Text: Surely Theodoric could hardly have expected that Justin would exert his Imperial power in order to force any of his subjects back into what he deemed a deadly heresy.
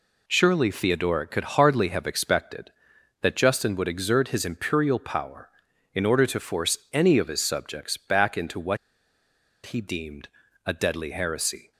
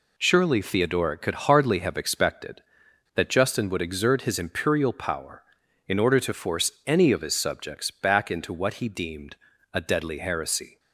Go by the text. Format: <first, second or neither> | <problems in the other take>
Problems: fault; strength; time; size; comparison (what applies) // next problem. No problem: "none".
second | pauses between "what" and "he"; noticeable; at 8.7 s; 0.88 s long // pauses between "deemed" and "a"; at 10.2 s; 0.38 s long; also in the second